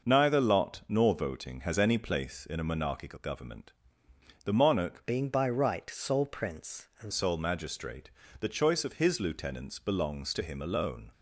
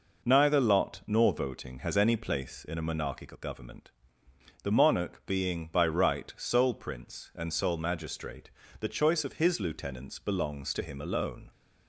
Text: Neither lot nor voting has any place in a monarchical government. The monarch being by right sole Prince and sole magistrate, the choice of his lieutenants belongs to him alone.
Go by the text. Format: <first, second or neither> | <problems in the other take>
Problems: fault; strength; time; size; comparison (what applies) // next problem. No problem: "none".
second | changes voice from "being" to "and"; from 5.0 to 7.1 s; 2.1 s long